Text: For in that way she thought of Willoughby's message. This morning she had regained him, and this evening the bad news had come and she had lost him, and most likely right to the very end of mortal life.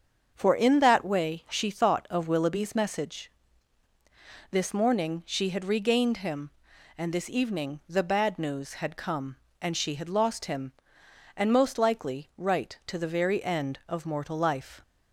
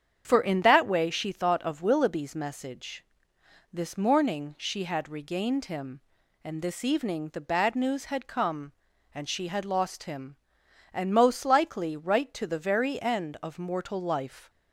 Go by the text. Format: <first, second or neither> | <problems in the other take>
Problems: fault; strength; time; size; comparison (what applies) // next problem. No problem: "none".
neither | starts louder than the rest; the same in both